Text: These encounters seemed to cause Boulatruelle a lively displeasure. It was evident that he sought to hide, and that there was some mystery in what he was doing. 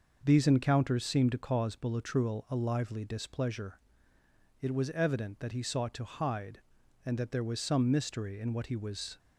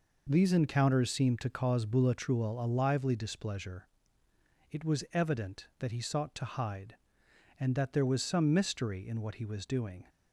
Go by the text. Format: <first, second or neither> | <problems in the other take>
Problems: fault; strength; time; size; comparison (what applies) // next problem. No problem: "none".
second | stops before "doing"; at 9.1 s